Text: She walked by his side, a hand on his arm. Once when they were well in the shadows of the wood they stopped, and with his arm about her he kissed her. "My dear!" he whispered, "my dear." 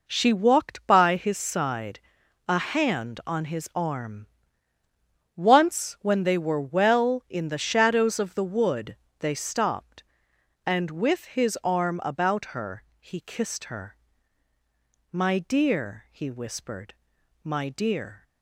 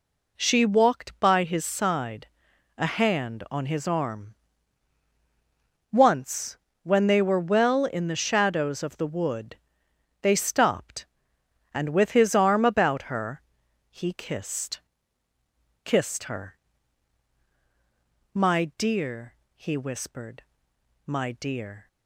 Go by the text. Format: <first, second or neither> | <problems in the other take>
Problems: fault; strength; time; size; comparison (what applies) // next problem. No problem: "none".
first | pauses between "Once" and "when"; slight; at 6.5 s; 0.26 s long // pauses between "wood" and "they"; noticeable; at 9.5 s; 0.66 s long; slight in the first // pauses between "her" and "he"; noticeable; at 13.4 s; 0.48 s long; slight in the first // says "kissed" twice; at 15.8 s